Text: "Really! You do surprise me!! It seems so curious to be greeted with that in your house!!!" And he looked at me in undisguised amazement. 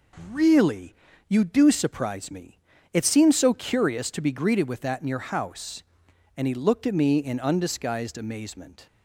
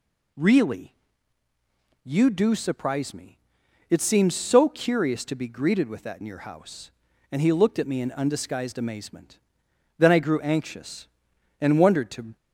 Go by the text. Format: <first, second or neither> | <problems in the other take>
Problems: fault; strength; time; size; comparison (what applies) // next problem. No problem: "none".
first | goes on to say "Then I grew anxious and wondered to"; strong; from 9.9 s on; 2.3 s long